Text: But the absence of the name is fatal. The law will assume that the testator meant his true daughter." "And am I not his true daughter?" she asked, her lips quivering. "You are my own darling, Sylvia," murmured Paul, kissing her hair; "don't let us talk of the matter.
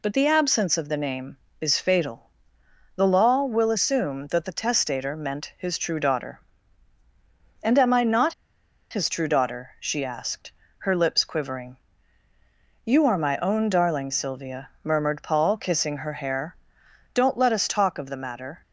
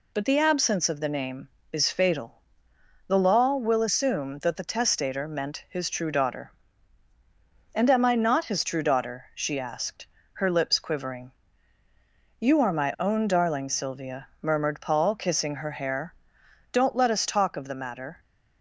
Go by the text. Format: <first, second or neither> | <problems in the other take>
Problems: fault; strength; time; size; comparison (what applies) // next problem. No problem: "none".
second | pauses between "not" and "his"; noticeable; at 8.3 s; 0.57 s long